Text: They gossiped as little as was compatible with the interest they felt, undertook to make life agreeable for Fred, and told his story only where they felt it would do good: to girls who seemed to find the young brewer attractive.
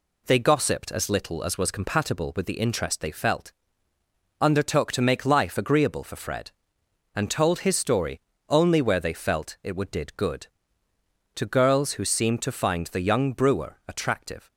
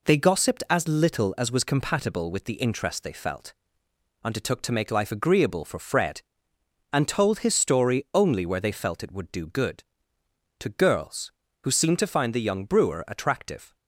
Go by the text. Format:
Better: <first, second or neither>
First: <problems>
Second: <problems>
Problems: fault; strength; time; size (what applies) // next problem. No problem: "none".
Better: second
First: pauses between "story" and "only"; slight; at 8.1 s; 0.28 s long // says "did" for "do"; at 9.9 s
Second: none